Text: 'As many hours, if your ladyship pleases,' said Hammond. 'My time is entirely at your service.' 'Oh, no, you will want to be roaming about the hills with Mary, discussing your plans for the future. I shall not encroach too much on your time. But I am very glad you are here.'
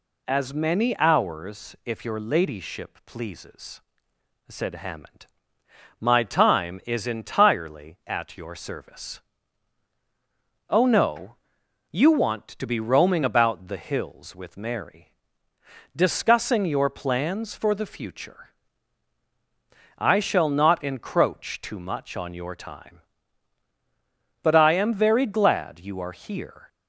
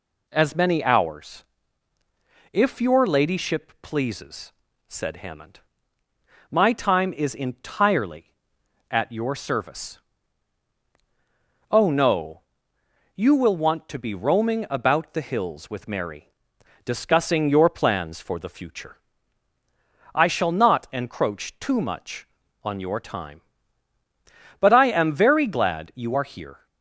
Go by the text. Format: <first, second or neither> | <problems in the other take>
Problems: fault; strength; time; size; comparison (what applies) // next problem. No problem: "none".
second | skips "will"; at 12.0 s